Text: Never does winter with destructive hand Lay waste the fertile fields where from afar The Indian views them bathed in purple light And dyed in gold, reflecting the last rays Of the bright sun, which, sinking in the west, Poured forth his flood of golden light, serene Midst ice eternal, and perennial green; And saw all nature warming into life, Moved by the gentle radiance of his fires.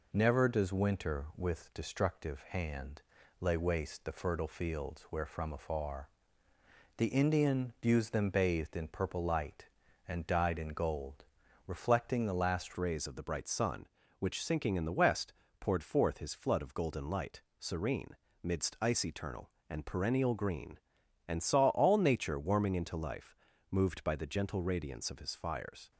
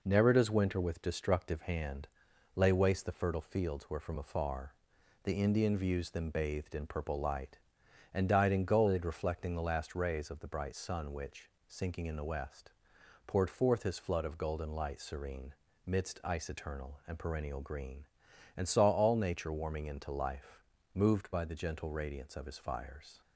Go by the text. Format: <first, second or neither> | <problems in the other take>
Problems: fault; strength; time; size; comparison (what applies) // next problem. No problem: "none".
second | pauses between "hand" and "Lay"; at 3.0 s; 0.38 s long; noticeable in the second // pauses between "afar" and "The"; noticeable; at 6.0 s; 0.88 s long; noticeable in the second // changes voice at "rays"; from 12.7 s on; 13.2 s long // pauses between "serene" and "Midst"; slight; at 18.0 s; 0.34 s long; slight in the second